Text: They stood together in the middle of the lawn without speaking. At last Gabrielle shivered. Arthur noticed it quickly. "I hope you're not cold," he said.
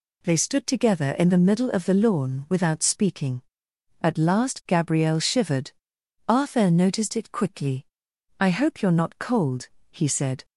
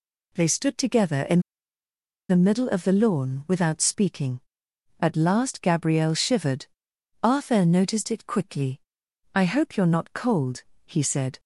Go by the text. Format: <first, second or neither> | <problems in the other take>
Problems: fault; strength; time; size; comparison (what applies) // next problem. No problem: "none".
first | pauses between "in" and "the"; noticeable; at 1.3 s; 0.89 s long